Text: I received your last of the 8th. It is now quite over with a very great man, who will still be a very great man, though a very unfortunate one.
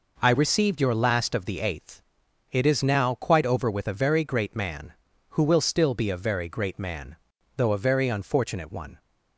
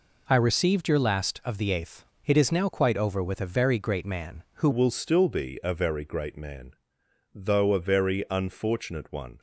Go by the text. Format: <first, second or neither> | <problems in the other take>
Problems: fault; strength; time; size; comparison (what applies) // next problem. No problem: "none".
first | changes voice at "will"; from 4.7 s on; 4.6 s long